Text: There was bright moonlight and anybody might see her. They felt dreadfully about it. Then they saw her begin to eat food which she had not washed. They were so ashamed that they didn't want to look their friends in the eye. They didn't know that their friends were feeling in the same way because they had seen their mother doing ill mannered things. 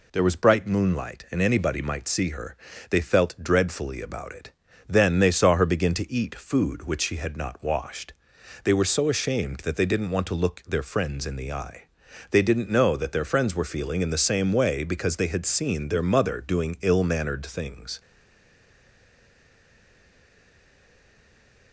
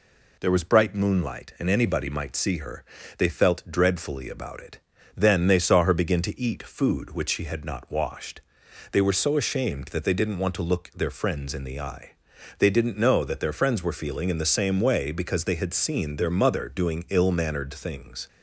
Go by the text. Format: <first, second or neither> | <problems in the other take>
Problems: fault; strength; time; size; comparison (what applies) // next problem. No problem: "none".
second | stays silent after the last word; strong; from 17.9 s on; 3.8 s long